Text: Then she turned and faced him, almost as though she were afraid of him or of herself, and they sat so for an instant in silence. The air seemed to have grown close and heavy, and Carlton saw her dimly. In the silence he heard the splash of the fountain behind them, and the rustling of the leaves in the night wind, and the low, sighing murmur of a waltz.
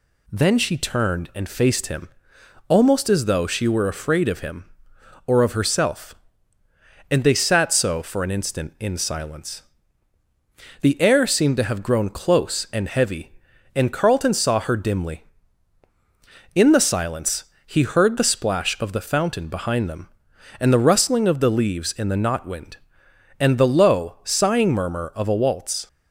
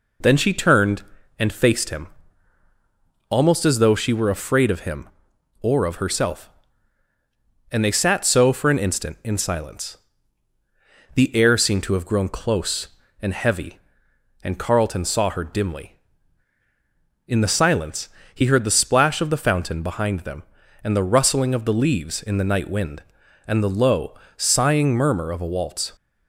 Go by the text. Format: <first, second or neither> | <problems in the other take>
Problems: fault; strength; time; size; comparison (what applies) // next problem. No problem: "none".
second | pauses between "silence" and "he"; slight; at 17.4 s; 0.20 s long; slight in the second // says "knot" for "night"; at 22.1 s